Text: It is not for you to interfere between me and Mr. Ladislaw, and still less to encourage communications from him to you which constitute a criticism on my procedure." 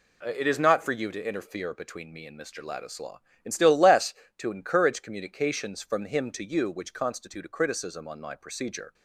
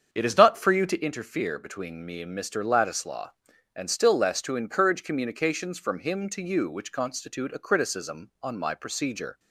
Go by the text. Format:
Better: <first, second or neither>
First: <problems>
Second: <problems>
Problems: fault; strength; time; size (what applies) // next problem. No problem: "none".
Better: first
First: none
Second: starts louder than the rest; strong; until 1.1 s; 7.5 dB